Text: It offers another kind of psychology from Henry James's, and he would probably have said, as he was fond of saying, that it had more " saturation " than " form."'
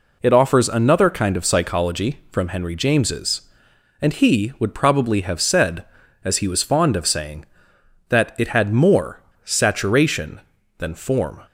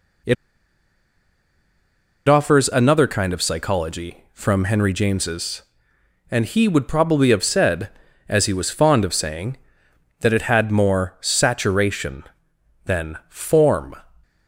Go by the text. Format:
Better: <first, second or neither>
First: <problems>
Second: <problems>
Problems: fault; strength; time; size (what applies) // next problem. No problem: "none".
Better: first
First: none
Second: pauses between "It" and "offers"; strong; at 0.3 s; 1.9 s long